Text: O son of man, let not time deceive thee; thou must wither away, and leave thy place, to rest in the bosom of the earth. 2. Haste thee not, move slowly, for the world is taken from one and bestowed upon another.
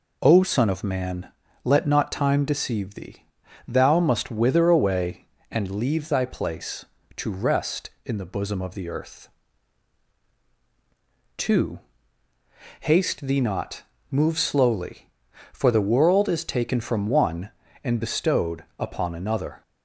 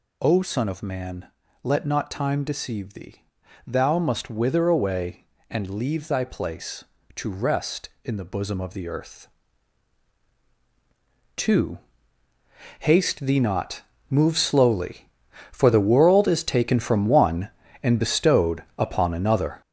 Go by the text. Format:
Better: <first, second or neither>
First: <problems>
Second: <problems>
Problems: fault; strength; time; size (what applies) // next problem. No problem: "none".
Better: first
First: pauses between "bestowed" and "upon"; slight; at 18.6 s; 0.16 s long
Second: gets louder; strong; throughout; 7.5 dB // pauses between "bestowed" and "upon"; slight; at 18.6 s; 0.16 s long